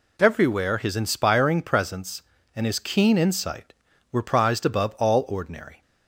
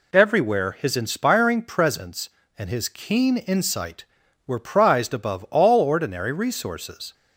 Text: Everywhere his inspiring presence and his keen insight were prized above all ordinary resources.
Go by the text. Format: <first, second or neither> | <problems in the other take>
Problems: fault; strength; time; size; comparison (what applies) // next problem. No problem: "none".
second | stops before "resources"; at 5.8 s